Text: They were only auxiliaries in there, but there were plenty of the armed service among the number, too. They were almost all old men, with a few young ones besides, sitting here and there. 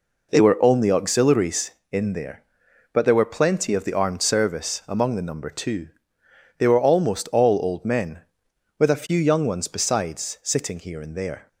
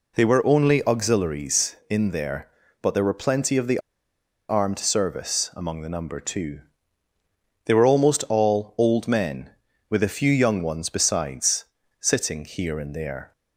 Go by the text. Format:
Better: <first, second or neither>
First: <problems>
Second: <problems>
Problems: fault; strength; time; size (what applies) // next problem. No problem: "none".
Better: first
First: none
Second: pauses between "the" and "armed"; noticeable; at 3.7 s; 0.69 s long